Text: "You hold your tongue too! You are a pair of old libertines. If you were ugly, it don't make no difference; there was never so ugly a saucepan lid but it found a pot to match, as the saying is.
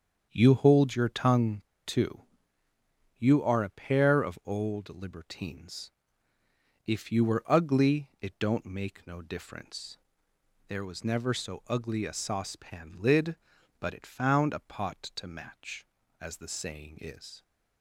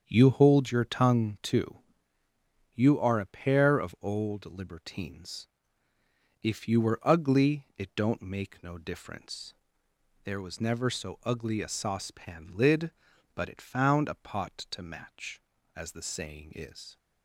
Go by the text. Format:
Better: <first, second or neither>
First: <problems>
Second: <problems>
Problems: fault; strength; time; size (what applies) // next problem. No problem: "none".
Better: second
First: starts louder than the rest; strong; until 1.3 s; 7.5 dB // pauses between "tongue" and "too"; slight; at 1.6 s; 0.22 s long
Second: starts louder than the rest; strong; until 1.0 s; 7.5 dB